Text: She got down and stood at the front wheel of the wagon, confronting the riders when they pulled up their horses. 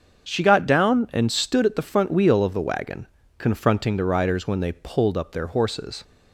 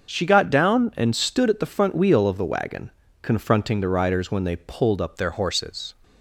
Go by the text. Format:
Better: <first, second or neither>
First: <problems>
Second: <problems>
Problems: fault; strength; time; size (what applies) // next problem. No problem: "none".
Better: first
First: starts louder than the rest; until 1.3 s; 6.5 dB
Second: starts louder than the rest; until 1.1 s; 6 dB // changes voice at "their"; from 5.1 s on; 0.8 s long